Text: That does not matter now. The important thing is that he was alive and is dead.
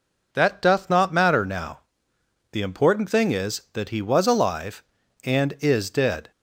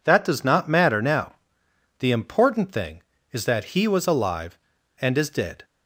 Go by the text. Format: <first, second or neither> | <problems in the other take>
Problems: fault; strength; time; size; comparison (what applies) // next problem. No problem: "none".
second | says "doth" for "does"; at 0.6 s